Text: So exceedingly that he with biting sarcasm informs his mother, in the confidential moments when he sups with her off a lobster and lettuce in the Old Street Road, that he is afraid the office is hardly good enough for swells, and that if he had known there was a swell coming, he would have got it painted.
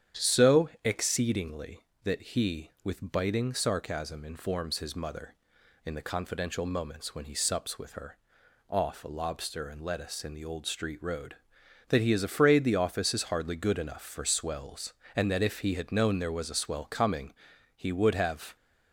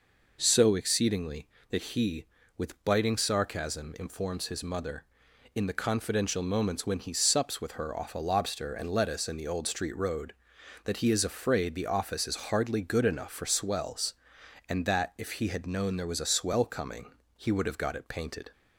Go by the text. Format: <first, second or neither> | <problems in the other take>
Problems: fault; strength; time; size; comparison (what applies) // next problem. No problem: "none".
second | starts louder than the rest; strong; until 1.3 s; 9.5 dB // pauses between "her" and "off"; noticeable; at 8.1 s; 0.54 s long // stops before "got it painted"; at 18.5 s